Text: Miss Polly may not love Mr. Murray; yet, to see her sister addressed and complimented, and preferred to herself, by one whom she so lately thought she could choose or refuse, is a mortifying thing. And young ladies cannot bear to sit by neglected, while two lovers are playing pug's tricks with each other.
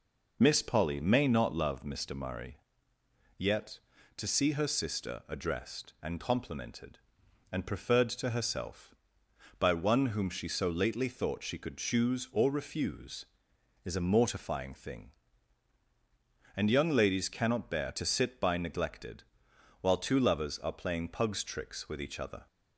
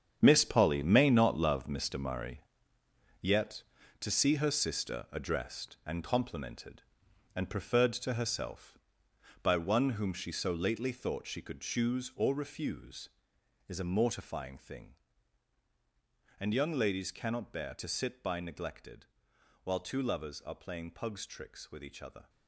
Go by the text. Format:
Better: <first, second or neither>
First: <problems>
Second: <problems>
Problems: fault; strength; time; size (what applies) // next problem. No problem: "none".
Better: first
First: none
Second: gets quieter; strong; throughout; 12 dB